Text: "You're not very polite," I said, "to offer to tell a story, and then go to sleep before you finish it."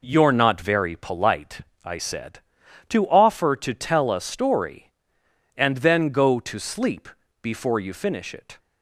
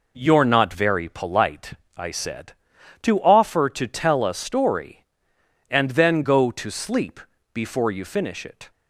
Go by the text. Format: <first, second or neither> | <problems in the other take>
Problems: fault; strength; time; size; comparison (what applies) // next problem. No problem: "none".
neither | pauses between "sleep" and "before"; slight; the same in both